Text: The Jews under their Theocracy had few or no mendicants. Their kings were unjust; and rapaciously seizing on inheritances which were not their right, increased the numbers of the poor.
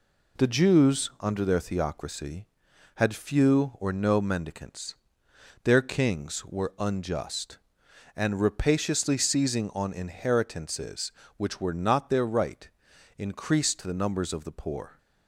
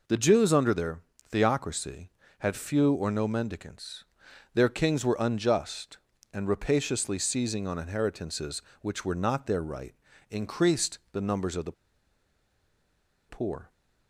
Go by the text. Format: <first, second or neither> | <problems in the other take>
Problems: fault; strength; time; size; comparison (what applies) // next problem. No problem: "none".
first | pauses between "their" and "Theocracy"; slight; at 1.0 s; 0.28 s long // pauses between "the" and "poor"; strong; at 11.7 s; 1.5 s long